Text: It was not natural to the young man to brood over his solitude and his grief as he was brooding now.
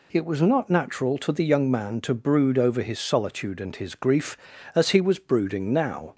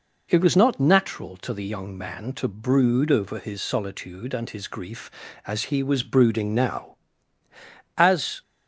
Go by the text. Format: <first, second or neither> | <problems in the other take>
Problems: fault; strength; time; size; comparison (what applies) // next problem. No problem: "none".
first | goes on to say "As"; slight; from 7.9 s on; 0.44 s long